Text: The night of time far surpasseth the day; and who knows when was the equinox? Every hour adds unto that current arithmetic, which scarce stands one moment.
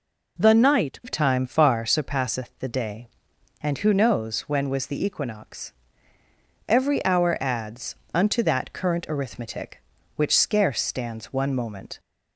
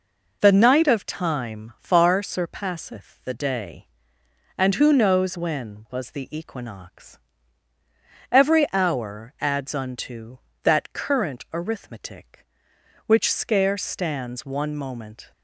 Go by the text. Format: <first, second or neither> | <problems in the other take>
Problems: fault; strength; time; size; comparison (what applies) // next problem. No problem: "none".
second | changes voice at "of"; from 1.0 s on; 10.9 s long // pauses between "adds" and "unto"; slight; at 7.9 s; 0.18 s long